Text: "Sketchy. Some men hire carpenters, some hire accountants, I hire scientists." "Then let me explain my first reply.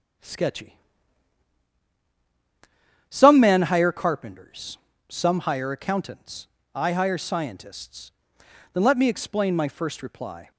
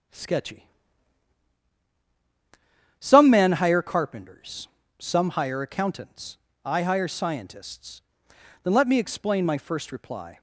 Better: neither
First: starts louder than the rest; strong; until 3.5 s; 8.5 dB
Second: starts louder than the rest; strong; until 3.4 s; 8.5 dB

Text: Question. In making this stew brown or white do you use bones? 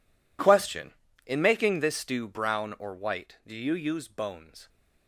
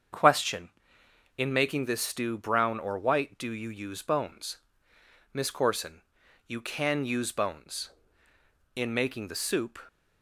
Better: first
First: none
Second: starts louder than the rest; strong; until 1.8 s; 7 dB // goes on to say "MISS CORSON You can use bones In making the soup"; strong; from 5.3 s on; 4.4 s long

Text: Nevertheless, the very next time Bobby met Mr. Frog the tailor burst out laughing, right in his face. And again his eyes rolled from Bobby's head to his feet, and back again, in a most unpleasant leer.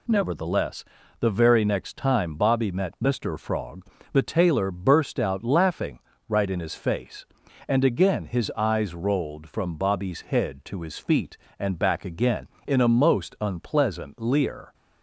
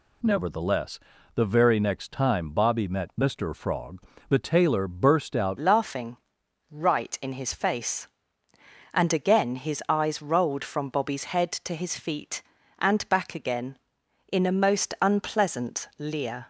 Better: first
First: pauses between "Frog" and "the"; slight; at 3.8 s; 0.28 s long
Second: pauses between "Frog" and "the"; slight; at 3.9 s; 0.28 s long // changes voice at "laughing"; from 5.5 s on; 10.9 s long

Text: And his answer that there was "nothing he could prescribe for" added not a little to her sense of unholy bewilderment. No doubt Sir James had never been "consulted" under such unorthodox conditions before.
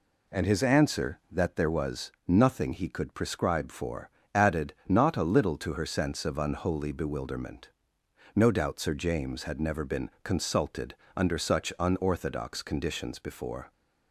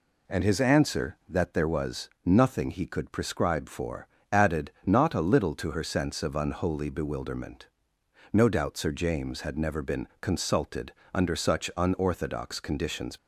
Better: first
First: pauses between "for" and "added"; slight; at 4.0 s; 0.24 s long // pauses between "consulted" and "under"; slight; at 10.9 s; 0.22 s long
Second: pauses between "for" and "added"; slight; at 4.0 s; 0.24 s long // pauses between "consulted" and "under"; slight; at 10.9 s; 0.22 s long // stops before "before"; at 13.1 s

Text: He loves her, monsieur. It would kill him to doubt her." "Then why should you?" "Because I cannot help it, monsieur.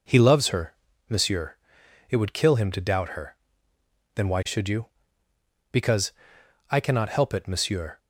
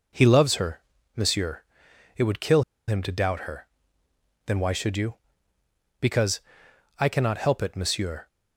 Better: first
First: pauses between "Because" and "I"; noticeable; at 6.1 s; 0.58 s long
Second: pauses between "kill" and "him"; slight; at 2.6 s; 0.26 s long // pauses between "Because" and "I"; noticeable; at 6.4 s; 0.58 s long

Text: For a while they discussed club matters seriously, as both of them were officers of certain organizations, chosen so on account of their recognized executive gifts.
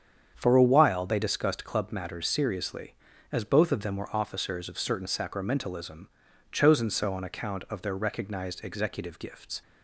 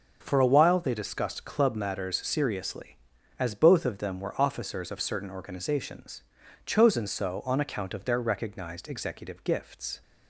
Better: second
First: starts louder than the rest; strong; until 1.3 s; 8 dB // says "sacramentalism" for "organizations"; at 5.0 s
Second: none

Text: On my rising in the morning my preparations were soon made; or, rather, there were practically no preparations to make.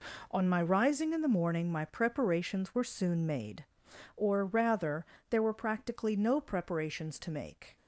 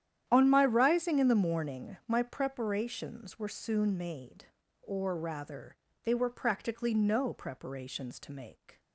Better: first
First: none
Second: starts louder than the rest; strong; until 1.2 s; 10 dB // says "they" for "there"; at 6.0 s

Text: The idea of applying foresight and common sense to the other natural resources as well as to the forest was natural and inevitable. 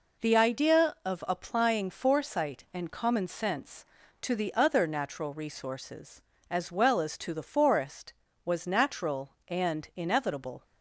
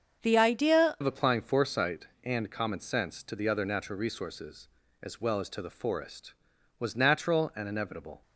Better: first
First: none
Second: starts louder than the rest; until 1.2 s; 7 dB // changes voice at "of"; from 1.0 s on; 7.2 s long

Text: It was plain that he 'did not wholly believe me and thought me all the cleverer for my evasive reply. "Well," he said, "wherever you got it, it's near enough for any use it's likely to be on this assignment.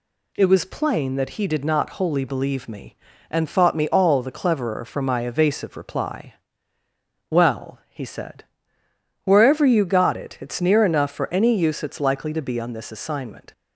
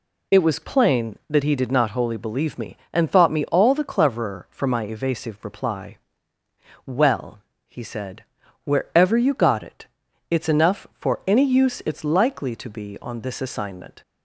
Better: first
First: none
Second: skips "near"; at 10.4 s

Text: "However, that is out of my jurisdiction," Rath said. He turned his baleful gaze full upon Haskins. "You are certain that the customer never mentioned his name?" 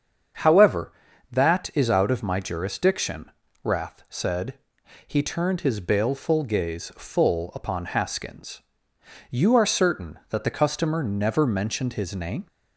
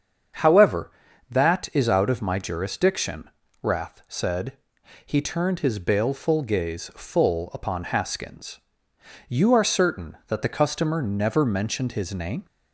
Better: neither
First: starts louder than the rest; strong; until 1.8 s; 7.5 dB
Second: starts louder than the rest; strong; until 1.8 s; 7.5 dB

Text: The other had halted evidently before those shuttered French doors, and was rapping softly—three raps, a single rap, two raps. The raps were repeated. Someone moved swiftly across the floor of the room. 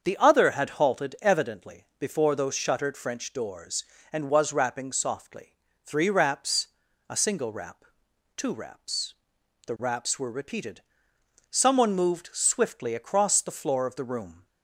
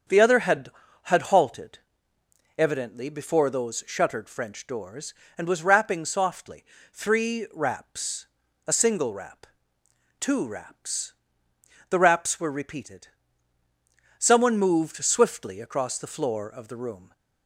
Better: first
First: starts louder than the rest; until 1.0 s; 7 dB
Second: starts louder than the rest; strong; until 1.4 s; 7 dB // says "had" twice; at 1.0 s // pauses between "halted" and "evidently"; noticeable; at 1.7 s; 0.80 s long

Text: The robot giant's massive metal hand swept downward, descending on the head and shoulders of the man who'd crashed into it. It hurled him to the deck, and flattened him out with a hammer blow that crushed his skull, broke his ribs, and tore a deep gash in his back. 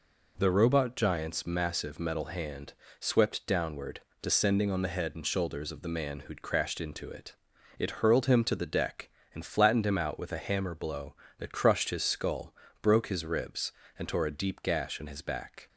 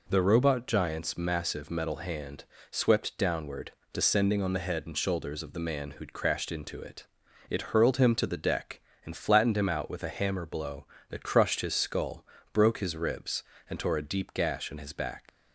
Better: first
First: pauses between "hand" and "swept"; slight; at 2.7 s; 0.26 s long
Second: pauses between "hand" and "swept"; slight; at 2.4 s; 0.26 s long // leaves "back" unfinished; at 15.2 s; 105 ms

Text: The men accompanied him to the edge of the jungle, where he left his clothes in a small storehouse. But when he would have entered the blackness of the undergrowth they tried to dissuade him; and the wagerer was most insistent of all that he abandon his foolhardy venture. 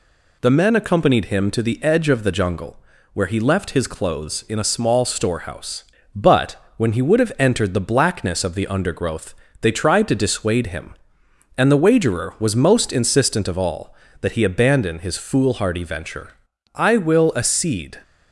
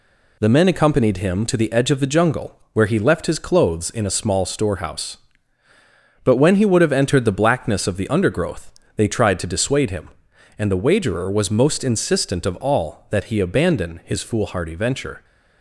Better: second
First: pauses between "But" and "when"; slight; at 6.5 s; 0.20 s long // pauses between "undergrowth" and "they"; slight; at 9.3 s; 0.26 s long // goes on to say "I will accede"; noticeable; from 16.7 s on; 1.2 s long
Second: pauses between "undergrowth" and "they"; slight; at 8.7 s; 0.24 s long

